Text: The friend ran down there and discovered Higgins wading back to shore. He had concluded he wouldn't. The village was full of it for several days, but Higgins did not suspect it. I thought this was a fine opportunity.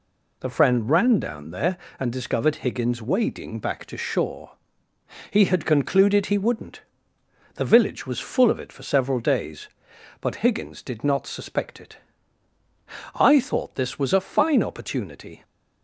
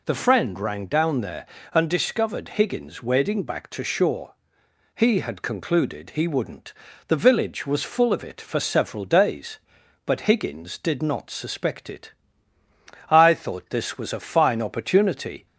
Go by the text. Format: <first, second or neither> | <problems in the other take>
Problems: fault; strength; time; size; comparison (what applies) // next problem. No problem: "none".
first | says "rang" for "ran"; at 0.5 s